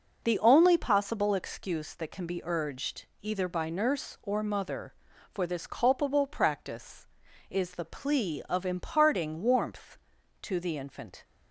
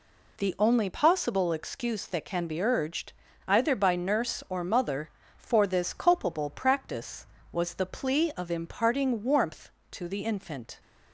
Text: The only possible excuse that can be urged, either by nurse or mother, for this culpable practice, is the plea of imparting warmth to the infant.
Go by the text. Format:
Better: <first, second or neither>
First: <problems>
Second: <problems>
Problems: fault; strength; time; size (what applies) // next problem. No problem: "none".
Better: first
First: none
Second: says "was" for "is"; at 7.5 s